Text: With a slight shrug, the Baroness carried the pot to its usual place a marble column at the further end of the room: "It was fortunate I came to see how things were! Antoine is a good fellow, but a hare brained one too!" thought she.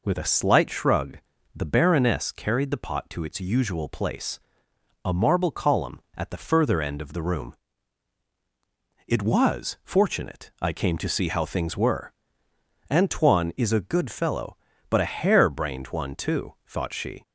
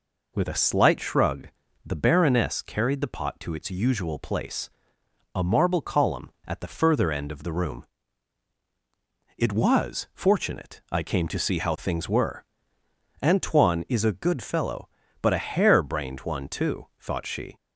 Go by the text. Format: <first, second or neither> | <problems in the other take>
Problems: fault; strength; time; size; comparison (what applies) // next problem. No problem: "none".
neither | pauses between "place" and "a"; noticeable; the same in both